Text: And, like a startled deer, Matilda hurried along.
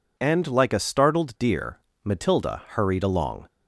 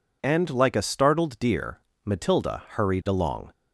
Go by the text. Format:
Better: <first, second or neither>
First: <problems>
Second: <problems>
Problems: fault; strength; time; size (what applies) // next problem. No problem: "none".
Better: neither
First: none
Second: none